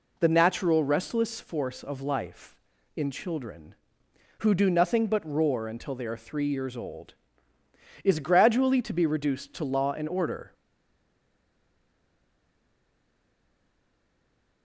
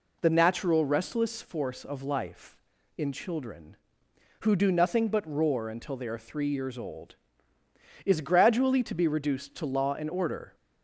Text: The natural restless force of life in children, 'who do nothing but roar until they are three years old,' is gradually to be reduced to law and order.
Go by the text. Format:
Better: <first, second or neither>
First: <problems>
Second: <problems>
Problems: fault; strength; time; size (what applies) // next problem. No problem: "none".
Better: second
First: stays silent after the last word; strong; from 10.5 s on; 4.1 s long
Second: none